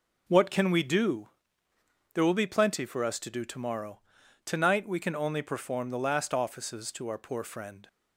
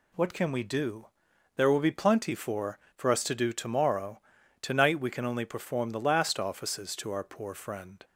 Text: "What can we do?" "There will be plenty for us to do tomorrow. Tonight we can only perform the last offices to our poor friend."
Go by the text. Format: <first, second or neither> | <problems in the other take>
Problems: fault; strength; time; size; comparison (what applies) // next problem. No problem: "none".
first | says "for" twice; at 2.9 s